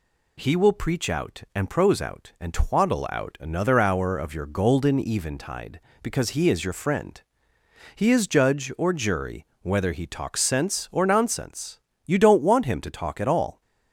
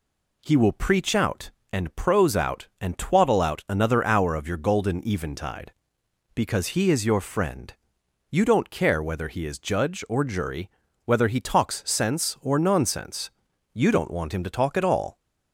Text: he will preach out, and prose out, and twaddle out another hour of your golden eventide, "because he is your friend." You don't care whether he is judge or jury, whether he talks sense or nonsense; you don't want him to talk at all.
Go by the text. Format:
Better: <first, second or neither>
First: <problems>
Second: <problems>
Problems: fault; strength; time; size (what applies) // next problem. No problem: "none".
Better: second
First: skips "You don't care whether"; at 7.5 s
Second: none